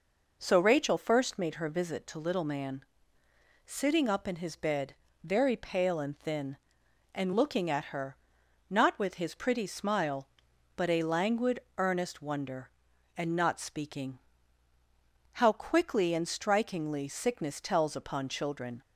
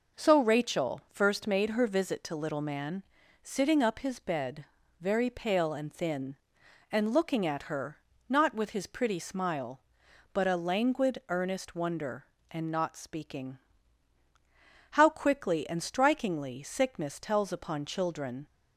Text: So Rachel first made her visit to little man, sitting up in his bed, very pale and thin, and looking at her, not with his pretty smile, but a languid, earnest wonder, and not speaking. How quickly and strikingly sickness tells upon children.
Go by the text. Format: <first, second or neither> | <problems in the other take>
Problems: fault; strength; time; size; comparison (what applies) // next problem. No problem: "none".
first | skips "in"; at 3.9 s